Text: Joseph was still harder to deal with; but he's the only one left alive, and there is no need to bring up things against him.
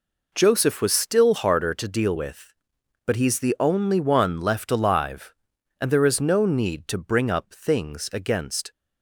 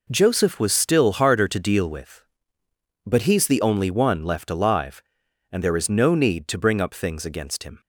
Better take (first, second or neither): second